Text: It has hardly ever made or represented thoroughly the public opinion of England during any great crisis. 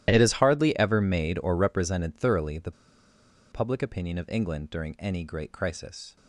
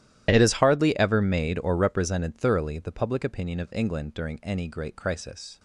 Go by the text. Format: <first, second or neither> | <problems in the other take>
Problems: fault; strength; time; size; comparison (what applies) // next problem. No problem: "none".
second | starts louder than the rest; strong; until 1.1 s; 12.5 dB; strong in the second // pauses between "the" and "public"; noticeable; at 2.7 s; 0.80 s long